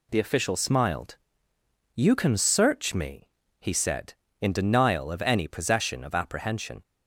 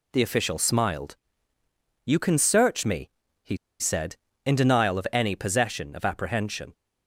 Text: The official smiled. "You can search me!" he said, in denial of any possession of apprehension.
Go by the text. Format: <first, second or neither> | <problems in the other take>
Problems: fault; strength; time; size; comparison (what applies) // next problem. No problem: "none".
first | pauses between "he" and "said"; slight; at 3.5 s; 0.23 s long